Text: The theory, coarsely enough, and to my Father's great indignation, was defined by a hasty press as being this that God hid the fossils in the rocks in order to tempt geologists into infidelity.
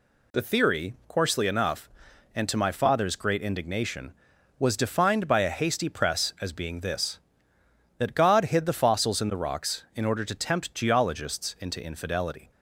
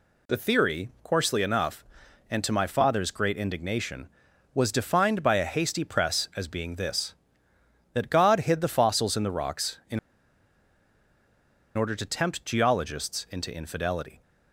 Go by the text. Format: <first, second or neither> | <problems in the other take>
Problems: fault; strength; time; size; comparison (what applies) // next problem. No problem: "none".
first | pauses between "in" and "order"; strong; at 9.9 s; 1.7 s long